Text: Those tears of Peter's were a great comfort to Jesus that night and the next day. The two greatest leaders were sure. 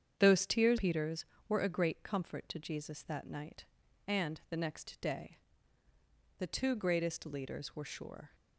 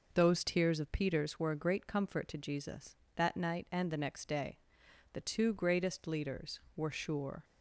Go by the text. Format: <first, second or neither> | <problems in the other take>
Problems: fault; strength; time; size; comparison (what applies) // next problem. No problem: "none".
second | starts louder than the rest; strong; until 1.1 s; 8 dB // skips "of"; at 0.7 s